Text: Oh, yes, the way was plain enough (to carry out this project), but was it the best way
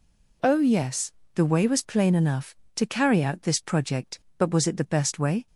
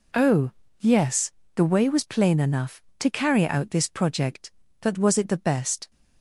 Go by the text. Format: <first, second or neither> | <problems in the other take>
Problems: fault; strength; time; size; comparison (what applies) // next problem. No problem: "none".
first | stops before "way"; at 5.9 s